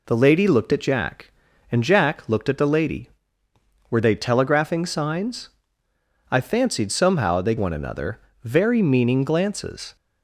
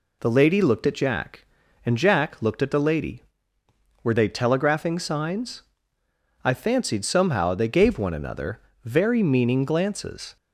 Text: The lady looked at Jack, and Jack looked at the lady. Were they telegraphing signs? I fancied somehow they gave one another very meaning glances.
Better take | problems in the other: second | skips "gave"; at 7.5 s // pauses between "another" and "very"; slight; at 8.1 s; 0.24 s long; slight in the second

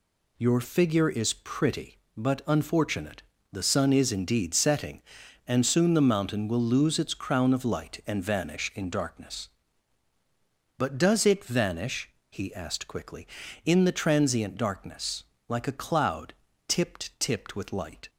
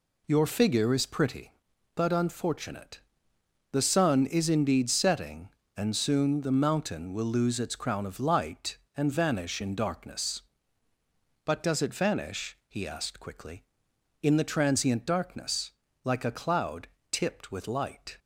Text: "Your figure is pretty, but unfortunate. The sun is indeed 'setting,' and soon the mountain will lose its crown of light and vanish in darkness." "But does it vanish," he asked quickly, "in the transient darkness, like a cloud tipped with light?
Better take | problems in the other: second | pauses between "cloud" and "tipped"; slight; at 16.3 s; 0.34 s long; slight in the second // says "tipped" twice; at 17.1 s

